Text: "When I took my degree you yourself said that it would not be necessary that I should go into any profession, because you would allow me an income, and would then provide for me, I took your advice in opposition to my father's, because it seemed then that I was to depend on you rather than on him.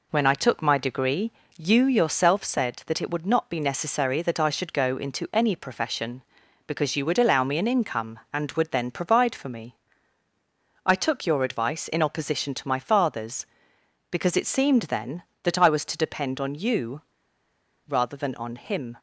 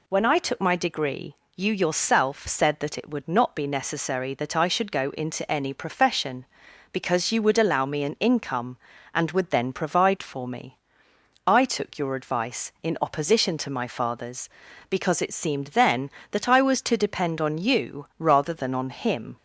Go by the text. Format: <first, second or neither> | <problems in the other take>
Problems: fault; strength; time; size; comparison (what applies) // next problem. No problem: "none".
second | pauses between "degree" and "you"; slight; at 1.3 s; 0.24 s long; slight in the second // pauses between "you" and "rather"; noticeable; at 17.0 s; 0.86 s long